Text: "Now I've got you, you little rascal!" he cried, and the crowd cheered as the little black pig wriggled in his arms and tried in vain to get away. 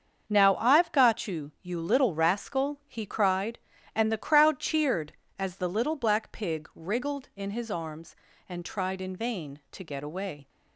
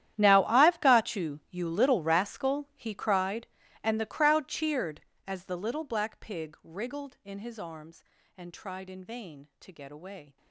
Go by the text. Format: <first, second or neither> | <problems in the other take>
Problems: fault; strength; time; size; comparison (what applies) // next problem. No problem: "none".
first | gets quieter; strong; throughout; 19 dB // starts louder than the rest; strong; until 1.1 s; 11.5 dB; also in the first